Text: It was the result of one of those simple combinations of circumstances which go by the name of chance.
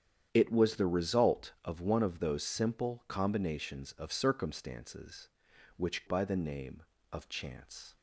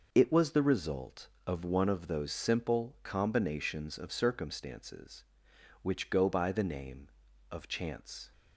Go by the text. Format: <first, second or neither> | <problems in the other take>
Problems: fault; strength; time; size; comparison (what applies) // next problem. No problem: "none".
second | starts louder than the rest; strong; until 1.3 s; 9 dB // skips "go"; at 6.0 s